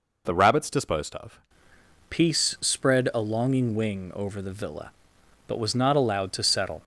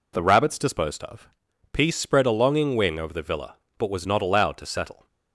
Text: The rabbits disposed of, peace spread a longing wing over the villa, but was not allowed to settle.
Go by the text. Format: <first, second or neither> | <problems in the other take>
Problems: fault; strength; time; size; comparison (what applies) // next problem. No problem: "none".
second | changes voice at "peace"; from 2.1 s on; 4.7 s long